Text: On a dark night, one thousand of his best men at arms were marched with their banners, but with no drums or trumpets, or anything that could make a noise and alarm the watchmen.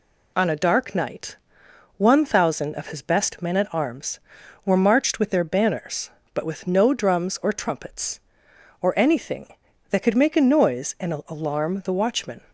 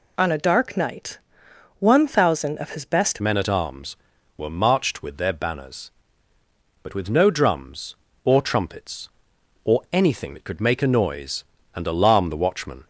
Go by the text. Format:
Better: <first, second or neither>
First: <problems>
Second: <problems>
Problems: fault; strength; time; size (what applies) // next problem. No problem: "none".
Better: first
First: none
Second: changes voice at "men"; from 3.1 s on; 9.7 s long